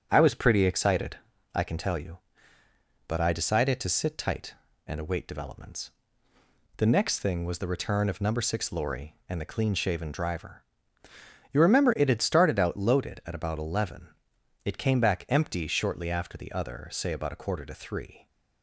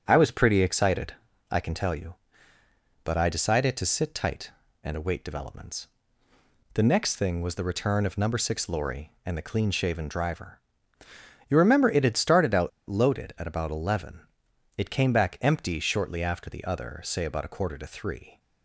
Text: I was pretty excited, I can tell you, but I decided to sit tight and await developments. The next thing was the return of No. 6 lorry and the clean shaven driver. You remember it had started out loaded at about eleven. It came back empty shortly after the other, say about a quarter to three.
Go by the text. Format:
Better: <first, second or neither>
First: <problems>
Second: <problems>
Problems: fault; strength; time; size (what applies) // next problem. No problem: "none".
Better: first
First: starts louder than the rest; strong; until 1.1 s; 8.5 dB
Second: starts louder than the rest; strong; until 1.0 s; 8.5 dB // pauses between "out" and "loaded"; slight; at 12.6 s; 0.19 s long